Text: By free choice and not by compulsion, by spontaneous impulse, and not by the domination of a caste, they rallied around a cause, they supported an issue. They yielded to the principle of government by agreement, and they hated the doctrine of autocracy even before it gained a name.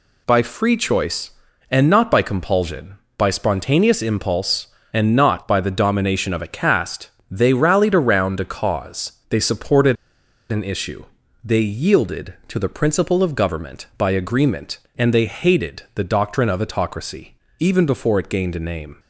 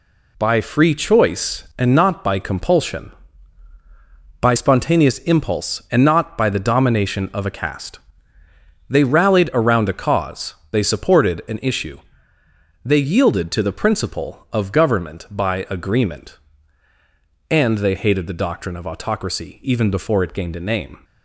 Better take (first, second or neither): second